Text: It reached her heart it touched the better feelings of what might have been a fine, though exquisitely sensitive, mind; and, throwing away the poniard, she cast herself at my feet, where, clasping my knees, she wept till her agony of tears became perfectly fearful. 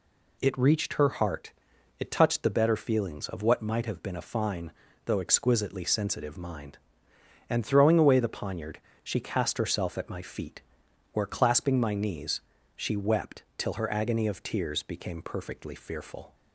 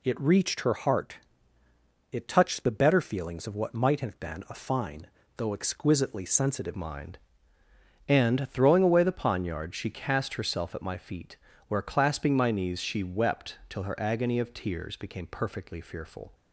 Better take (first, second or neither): first